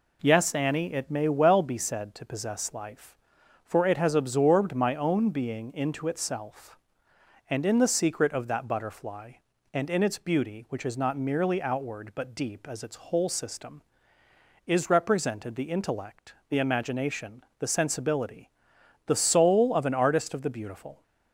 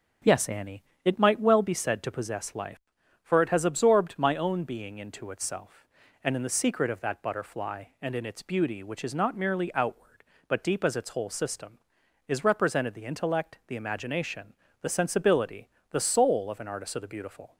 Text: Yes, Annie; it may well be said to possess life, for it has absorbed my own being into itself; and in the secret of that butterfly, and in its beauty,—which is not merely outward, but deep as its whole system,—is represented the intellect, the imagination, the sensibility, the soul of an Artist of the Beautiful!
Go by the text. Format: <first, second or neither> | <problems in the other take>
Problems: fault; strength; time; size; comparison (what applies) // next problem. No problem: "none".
first | says "might" for "may"; at 1.1 s